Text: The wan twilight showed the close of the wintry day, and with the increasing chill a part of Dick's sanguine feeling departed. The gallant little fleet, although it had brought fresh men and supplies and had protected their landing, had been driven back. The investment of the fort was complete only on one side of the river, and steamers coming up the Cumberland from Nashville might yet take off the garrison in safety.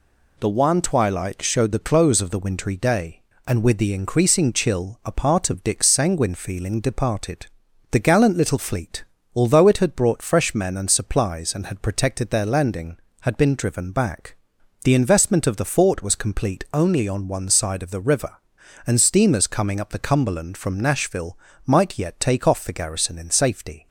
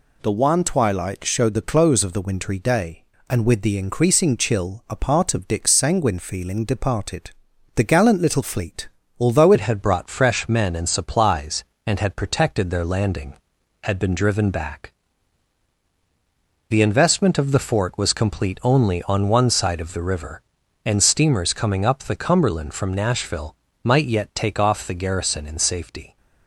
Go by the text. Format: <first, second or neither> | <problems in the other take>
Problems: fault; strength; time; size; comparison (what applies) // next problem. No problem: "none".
first | changes voice at "it"; from 9.5 s on; 16.6 s long // pauses between "Nashville" and "might"; slight; at 23.5 s; 0.30 s long; slight in the first